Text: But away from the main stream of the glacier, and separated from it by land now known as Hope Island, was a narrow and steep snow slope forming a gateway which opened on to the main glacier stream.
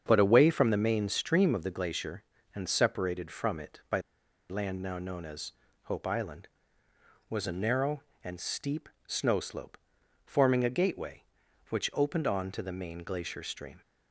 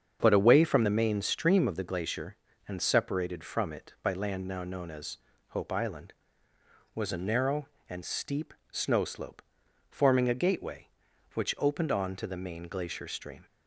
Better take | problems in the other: second | starts louder than the rest; strong; until 1.0 s; 7 dB; strong in the second // pauses between "by" and "land"; noticeable; at 3.9 s; 0.50 s long // pauses between "as" and "Hope"; slight; at 5.5 s; 0.32 s long; slight in the second // pauses between "steep" and "snow"; slight; at 8.8 s; 0.16 s long; slight in the second // pauses between "slope" and "forming"; noticeable; at 9.7 s; 0.48 s long; noticeable in the second

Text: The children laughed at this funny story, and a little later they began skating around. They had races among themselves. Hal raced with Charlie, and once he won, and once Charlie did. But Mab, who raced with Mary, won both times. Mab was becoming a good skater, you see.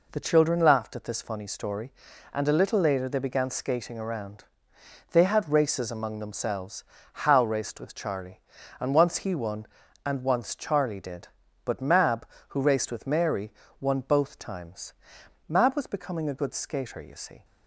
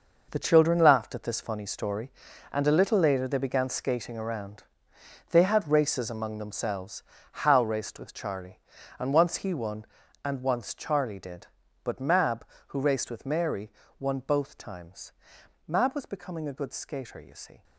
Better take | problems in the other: first | gets quieter; strong; throughout; 11 dB

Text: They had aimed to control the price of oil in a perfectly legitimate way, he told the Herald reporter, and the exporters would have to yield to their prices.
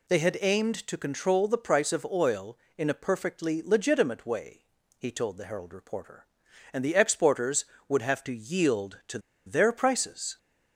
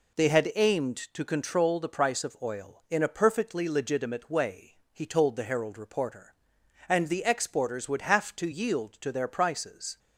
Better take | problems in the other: second | pauses between "to" and "their"; slight; at 9.1 s; 0.27 s long

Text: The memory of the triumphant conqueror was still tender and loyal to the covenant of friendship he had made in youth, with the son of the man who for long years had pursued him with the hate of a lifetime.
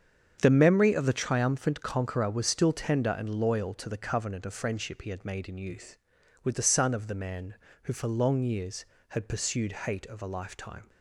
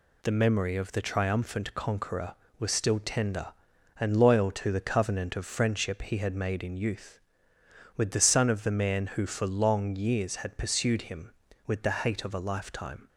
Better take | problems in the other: second | starts louder than the rest; strong; until 1.4 s; 7.5 dB // skips "him with the"; at 9.8 s

